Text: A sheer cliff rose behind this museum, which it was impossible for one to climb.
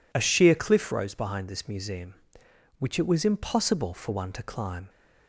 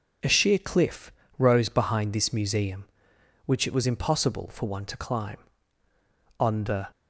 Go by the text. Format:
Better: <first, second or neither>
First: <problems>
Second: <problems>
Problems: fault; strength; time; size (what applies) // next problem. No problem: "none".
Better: first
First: none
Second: pauses between "cliff" and "rose"; slight; at 1.1 s; 0.26 s long // goes on to say "On the"; from 6.3 s on; 0.50 s long